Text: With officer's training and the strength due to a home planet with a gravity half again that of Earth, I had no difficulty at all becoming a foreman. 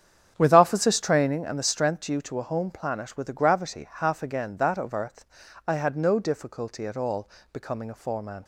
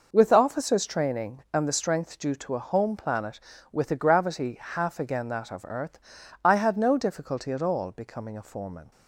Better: second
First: starts louder than the rest; strong; until 1.4 s; 8.5 dB // pauses between "all" and "becoming"; slight; at 7.2 s; 0.24 s long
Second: none

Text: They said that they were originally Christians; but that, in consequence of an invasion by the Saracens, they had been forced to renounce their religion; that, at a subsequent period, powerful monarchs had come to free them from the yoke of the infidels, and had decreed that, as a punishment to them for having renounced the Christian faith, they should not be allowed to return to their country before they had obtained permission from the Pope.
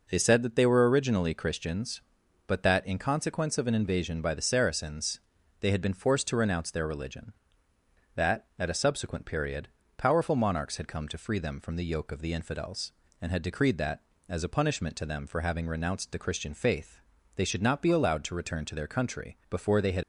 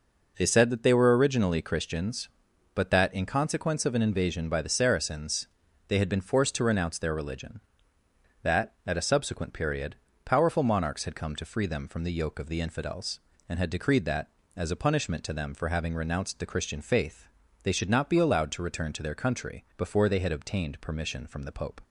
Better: second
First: stops before "obtained permission from the Pope"; at 20.0 s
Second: none

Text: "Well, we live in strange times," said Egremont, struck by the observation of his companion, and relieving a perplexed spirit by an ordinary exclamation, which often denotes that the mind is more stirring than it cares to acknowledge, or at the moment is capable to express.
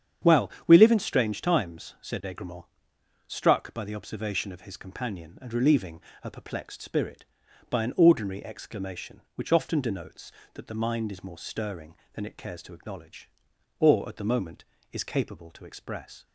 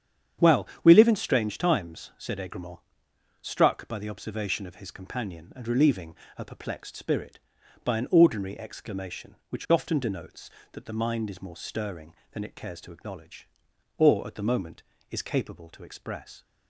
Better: neither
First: starts louder than the rest; strong; until 1.4 s; 8.5 dB // pauses between "relieving" and "a"; slight; at 6.0 s; 0.22 s long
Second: starts louder than the rest; strong; until 1.6 s; 8.5 dB // pauses between "relieving" and "a"; slight; at 6.1 s; 0.22 s long

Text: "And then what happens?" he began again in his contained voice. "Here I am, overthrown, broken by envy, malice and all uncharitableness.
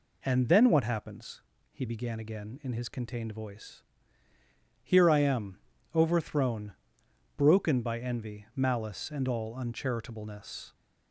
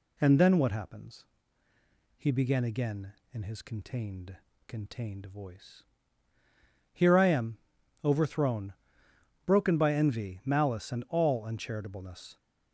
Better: first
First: none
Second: says "contained" twice; at 4.6 s

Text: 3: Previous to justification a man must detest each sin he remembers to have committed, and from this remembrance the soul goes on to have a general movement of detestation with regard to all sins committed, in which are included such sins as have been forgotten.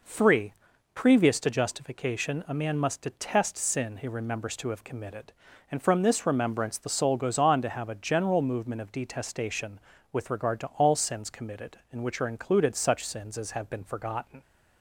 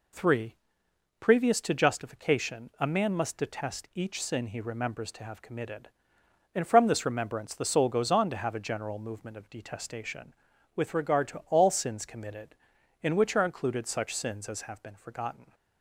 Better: second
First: skips "each"; at 3.5 s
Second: none

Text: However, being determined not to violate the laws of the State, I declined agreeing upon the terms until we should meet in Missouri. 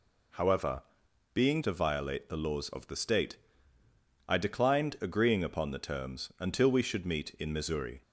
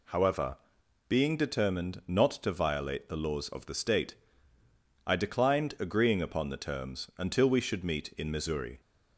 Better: second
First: skips "determined not"; at 1.6 s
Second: none

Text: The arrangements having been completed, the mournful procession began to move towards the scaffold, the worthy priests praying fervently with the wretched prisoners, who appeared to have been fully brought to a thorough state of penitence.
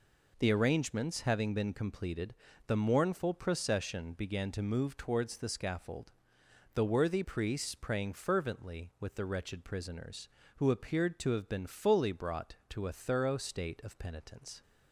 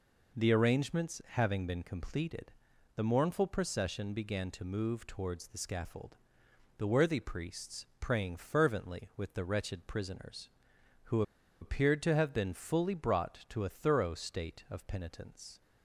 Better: first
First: none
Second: pauses between "priests" and "praying"; slight; at 7.8 s; 0.16 s long // pauses between "who" and "appeared"; at 11.2 s; 0.39 s long

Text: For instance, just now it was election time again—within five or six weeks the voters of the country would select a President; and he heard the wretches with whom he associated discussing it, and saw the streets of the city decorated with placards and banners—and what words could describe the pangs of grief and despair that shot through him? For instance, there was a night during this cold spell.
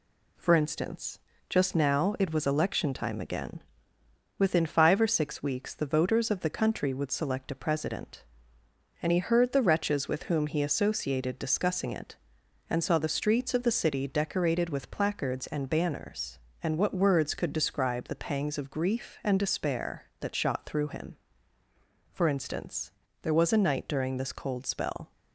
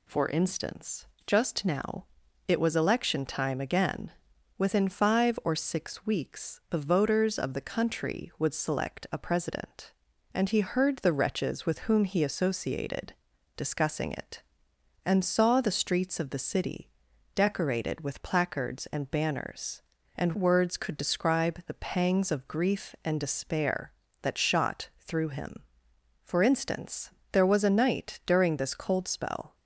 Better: first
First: none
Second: pauses between "now" and "it"; at 2.0 s; 0.42 s long // pauses between "associated" and "discussing"; noticeable; at 13.1 s; 0.46 s long // pauses between "city" and "decorated"; noticeable; at 16.8 s; 0.46 s long // skips "what"; at 20.3 s

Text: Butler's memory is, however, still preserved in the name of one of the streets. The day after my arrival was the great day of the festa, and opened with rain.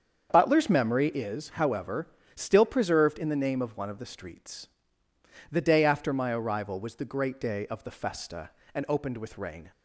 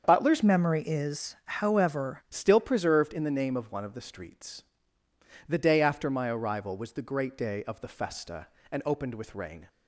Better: first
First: starts louder than the rest; strong; until 1.3 s; 7.5 dB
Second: starts louder than the rest; strong; until 1.0 s; 7 dB // changes voice from "memory" to "however"; from 0.4 to 2.2 s; 1.8 s long

